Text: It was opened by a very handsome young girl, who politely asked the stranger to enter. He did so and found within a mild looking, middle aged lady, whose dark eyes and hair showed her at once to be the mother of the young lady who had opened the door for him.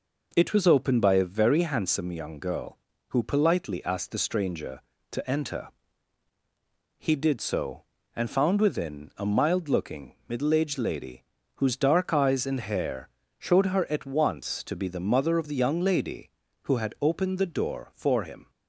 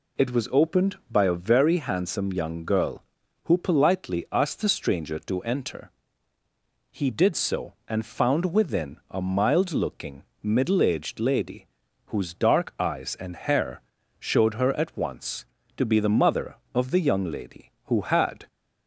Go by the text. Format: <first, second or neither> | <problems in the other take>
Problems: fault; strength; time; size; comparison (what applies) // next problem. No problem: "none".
first | pauses between "hair" and "showed"; slight; at 13.8 s; 0.36 s long; slight in the first // stops before "opened the door for him"; at 18.4 s